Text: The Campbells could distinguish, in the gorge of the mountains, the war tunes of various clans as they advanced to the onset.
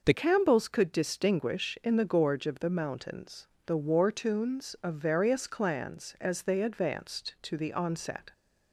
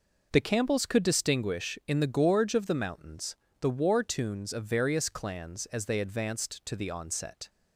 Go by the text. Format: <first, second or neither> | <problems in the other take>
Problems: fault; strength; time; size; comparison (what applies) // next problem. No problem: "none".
second | changes voice at "Campbells"; from 0.1 s on; 8.2 s long